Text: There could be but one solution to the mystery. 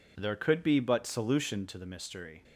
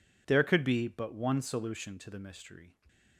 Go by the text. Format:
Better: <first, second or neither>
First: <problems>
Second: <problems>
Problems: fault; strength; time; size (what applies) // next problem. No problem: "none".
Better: second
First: skips "one"; at 1.0 s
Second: none